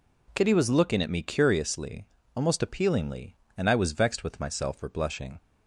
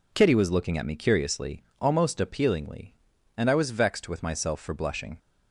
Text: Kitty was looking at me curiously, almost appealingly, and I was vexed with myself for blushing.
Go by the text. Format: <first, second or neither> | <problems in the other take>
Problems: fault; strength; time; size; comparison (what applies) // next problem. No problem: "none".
neither | none